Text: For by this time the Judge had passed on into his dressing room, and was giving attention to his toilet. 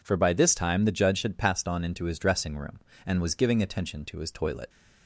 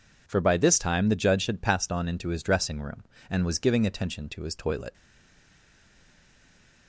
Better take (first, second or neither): first